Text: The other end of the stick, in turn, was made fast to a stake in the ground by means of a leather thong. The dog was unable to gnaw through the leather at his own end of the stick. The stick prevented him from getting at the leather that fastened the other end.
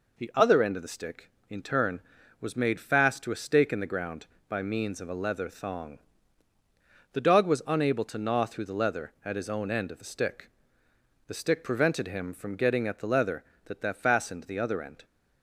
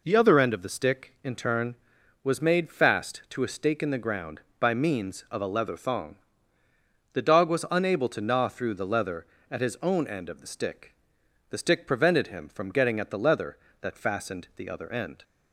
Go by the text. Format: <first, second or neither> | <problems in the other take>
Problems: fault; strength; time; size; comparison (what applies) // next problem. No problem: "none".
second | says "that" twice; at 13.8 s